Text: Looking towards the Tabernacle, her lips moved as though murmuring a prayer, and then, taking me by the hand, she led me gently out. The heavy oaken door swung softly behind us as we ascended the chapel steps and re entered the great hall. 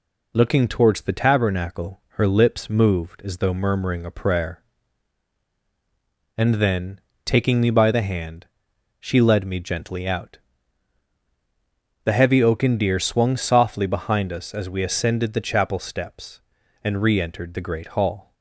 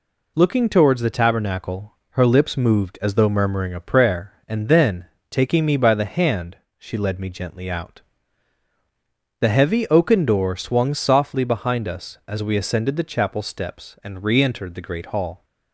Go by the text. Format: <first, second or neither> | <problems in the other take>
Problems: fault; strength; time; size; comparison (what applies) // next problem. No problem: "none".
second | says "deer" for "door"; at 12.7 s